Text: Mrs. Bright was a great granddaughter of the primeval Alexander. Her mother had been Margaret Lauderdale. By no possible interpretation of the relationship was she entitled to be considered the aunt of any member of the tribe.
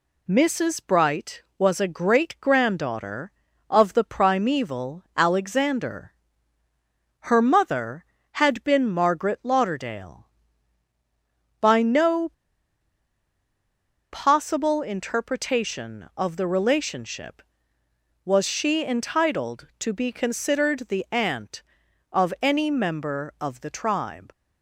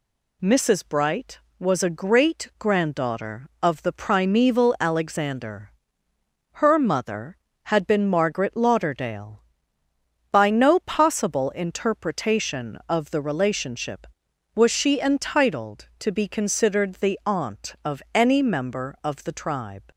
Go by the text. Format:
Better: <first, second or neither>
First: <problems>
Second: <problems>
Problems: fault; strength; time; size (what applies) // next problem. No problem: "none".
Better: second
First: pauses between "no" and "possible"; strong; at 12.2 s; 1.8 s long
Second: none